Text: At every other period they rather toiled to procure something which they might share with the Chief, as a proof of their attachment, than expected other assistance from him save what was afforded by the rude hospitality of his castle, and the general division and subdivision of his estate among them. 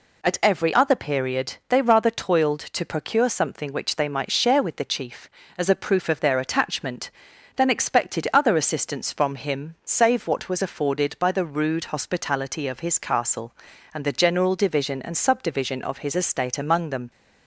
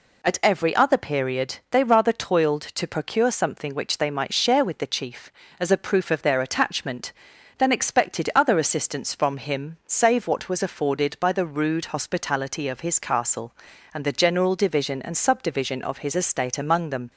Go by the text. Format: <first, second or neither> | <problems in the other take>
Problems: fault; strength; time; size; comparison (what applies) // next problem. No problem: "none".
neither | none